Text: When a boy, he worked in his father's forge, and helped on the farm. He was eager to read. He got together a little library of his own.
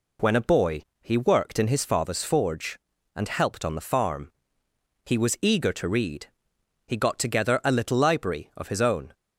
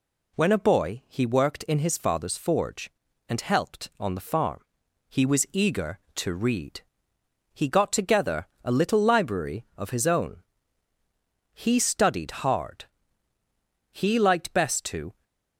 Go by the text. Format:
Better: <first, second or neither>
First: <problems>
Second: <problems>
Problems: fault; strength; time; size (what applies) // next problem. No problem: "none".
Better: first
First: none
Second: pauses between "together" and "a"; slight; at 8.4 s; 0.16 s long // goes on to say "He studied hard He liked best to"; strong; from 11.5 s on; 3.7 s long